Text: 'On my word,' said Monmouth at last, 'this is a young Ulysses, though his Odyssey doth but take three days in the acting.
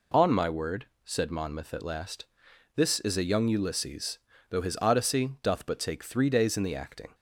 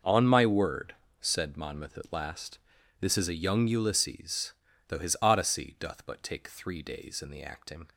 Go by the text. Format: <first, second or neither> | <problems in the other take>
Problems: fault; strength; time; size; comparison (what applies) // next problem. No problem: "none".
neither | none